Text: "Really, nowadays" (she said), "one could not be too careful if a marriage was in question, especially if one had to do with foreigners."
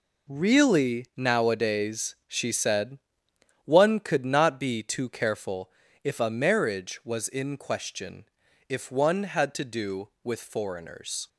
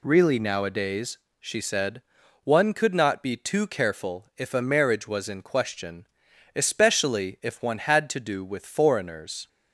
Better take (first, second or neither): second